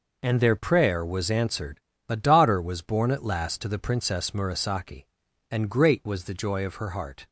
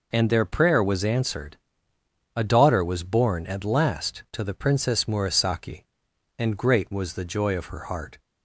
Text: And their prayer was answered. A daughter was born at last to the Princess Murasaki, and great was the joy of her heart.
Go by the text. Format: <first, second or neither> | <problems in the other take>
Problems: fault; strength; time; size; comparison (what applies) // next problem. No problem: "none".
neither | none